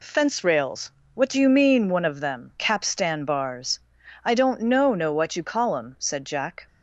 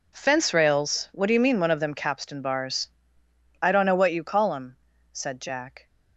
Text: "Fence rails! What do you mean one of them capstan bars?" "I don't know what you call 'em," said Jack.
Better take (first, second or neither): second